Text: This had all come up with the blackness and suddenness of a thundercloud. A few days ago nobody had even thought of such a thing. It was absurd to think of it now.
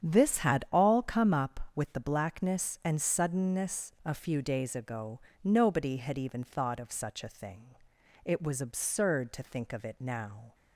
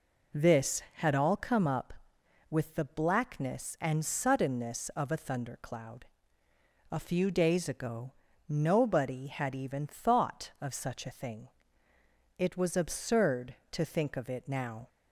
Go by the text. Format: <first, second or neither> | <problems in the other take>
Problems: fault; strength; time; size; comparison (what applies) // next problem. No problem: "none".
second | starts louder than the rest; strong; until 1.0 s; 8.5 dB // skips "of a thundercloud"; at 3.9 s // pauses between "ago" and "nobody"; slight; at 5.2 s; 0.24 s long; slight in the second